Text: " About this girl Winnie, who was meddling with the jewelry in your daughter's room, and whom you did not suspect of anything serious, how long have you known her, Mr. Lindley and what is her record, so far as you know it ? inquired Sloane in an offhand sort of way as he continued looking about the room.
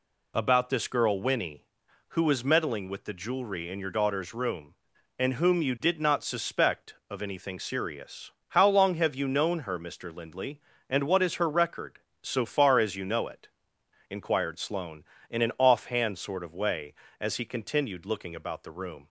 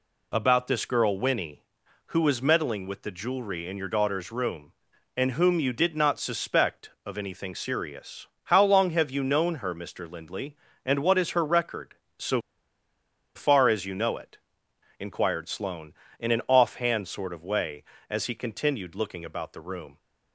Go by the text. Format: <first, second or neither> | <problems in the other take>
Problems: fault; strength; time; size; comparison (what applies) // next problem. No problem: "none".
first | pauses between "so" and "far"; noticeable; at 12.4 s; 0.94 s long